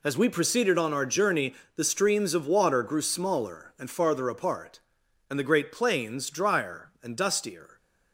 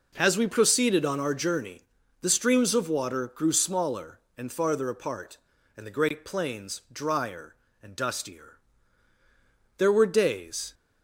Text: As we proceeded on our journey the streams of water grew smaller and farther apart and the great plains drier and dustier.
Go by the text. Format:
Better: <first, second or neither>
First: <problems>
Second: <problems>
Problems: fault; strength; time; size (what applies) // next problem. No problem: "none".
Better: first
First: pauses between "journey" and "the"; slight; at 1.5 s; 0.22 s long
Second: pauses between "journey" and "the"; at 1.8 s; 0.40 s long // goes on to say "There were days"; noticeable; from 9.7 s on; 0.96 s long